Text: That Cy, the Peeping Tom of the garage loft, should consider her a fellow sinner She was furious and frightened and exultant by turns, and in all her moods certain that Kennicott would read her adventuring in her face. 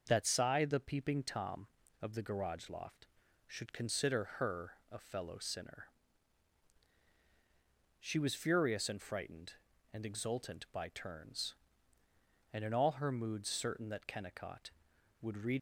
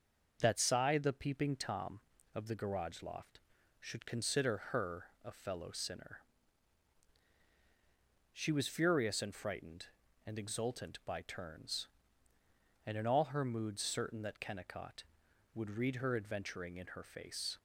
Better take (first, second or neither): second